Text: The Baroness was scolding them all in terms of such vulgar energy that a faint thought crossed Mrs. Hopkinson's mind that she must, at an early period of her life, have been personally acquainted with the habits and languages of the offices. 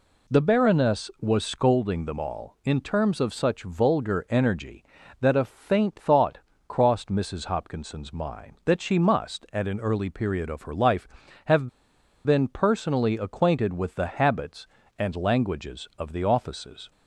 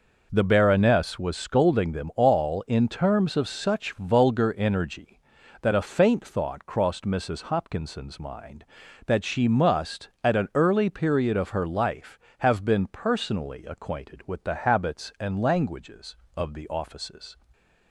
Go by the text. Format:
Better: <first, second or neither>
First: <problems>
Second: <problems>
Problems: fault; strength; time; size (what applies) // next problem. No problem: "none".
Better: second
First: pauses between "thought" and "crossed"; slight; at 6.3 s; 0.28 s long // pauses between "have" and "been"; noticeable; at 11.6 s; 0.56 s long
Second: none